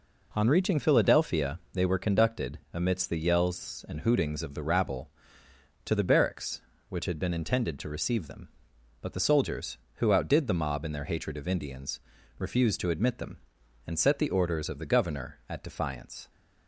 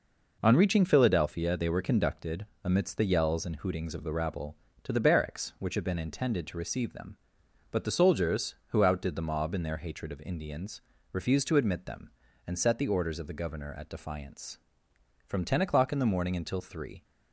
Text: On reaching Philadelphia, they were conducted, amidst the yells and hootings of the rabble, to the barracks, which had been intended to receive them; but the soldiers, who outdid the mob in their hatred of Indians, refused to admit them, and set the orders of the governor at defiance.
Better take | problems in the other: first | goes on to say "From ten o'clock in the morning until three"; strong; from 15.2 s on; 1.7 s long

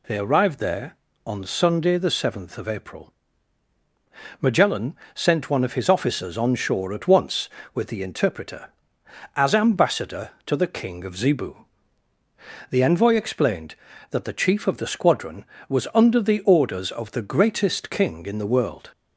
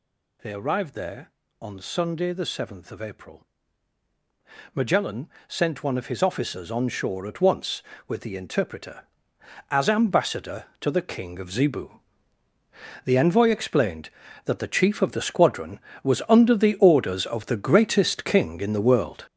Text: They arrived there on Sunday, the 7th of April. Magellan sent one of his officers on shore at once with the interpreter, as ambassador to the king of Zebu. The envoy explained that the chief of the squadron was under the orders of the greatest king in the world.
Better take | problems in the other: first | gets louder; strong; throughout; 8 dB // pauses between "Magellan" and "sent"; slight; at 5.2 s; 0.20 s long; slight in the first

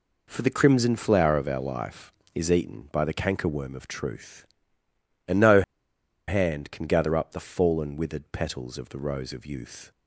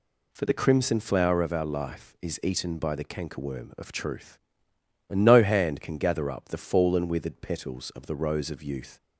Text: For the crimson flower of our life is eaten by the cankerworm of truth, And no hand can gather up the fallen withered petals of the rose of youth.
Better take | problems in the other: second | pauses between "no" and "hand"; noticeable; at 5.6 s; 0.65 s long

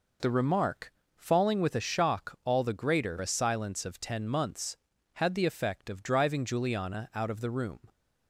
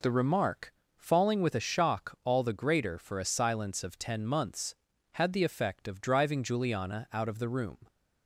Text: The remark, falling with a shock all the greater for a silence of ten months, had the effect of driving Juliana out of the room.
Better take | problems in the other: second | skips "for"; at 3.1 s

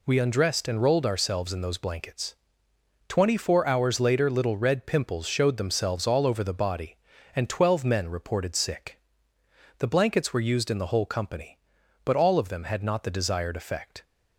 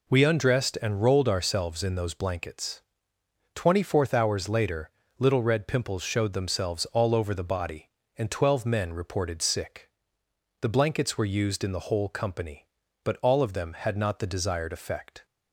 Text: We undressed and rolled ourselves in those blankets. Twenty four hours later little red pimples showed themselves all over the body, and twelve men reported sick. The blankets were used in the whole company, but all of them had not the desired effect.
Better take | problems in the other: first | says "fourth" for "four"; at 3.8 s // pauses between "later" and "little"; slight; at 4.8 s; 0.30 s long

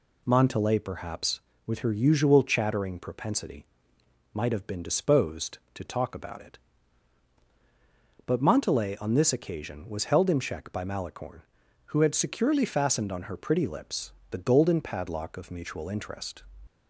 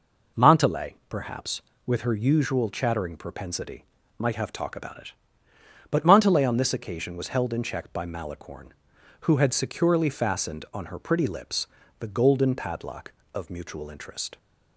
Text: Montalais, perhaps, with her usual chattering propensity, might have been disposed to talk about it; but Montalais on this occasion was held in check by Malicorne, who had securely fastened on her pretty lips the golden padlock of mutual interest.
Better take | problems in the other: first | skips "been disposed to"; at 4.5 s // pauses between "lips" and "the"; slight; at 11.6 s; 0.32 s long; slight in the first

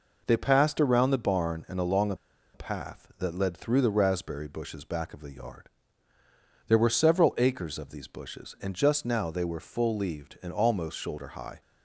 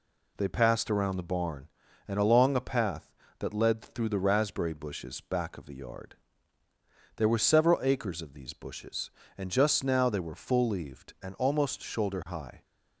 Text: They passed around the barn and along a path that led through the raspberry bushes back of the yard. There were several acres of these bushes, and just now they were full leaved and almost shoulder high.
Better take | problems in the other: second | pauses between "a" and "path"; at 2.1 s; 0.38 s long

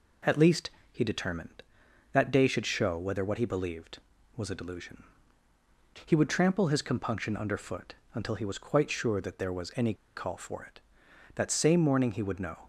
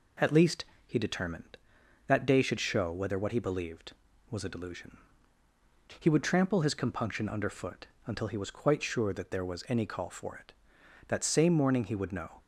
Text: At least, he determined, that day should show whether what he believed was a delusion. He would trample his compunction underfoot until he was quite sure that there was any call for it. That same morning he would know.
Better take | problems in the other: second | pauses between "underfoot" and "until"; slight; at 7.9 s; 0.20 s long; slight in the second // pauses between "any" and "call"; slight; at 9.9 s; 0.22 s long

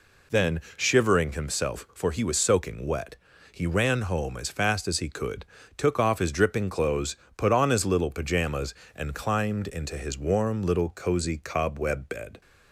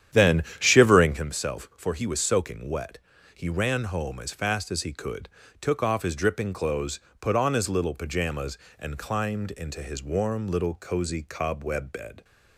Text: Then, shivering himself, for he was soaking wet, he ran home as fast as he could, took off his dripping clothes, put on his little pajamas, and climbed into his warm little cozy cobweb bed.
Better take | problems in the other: first | starts louder than the rest; strong; until 1.3 s; 10 dB

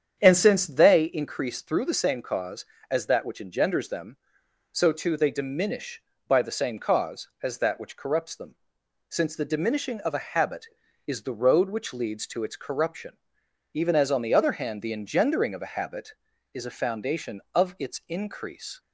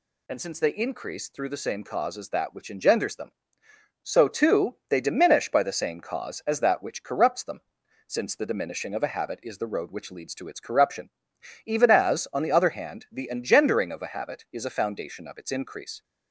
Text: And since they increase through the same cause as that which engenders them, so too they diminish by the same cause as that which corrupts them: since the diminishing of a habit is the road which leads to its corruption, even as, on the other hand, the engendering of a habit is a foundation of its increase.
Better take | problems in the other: second | starts louder than the rest; strong; until 1.1 s; 8 dB

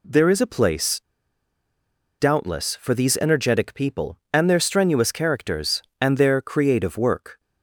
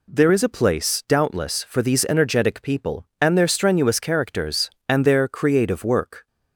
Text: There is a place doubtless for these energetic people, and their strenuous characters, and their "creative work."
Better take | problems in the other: second | pauses between "place" and "doubtless"; at 0.9 s; 1.1 s long

